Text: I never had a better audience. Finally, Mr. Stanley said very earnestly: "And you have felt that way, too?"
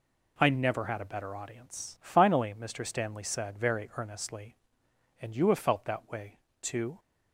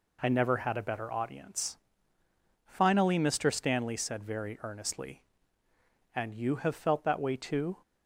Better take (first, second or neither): neither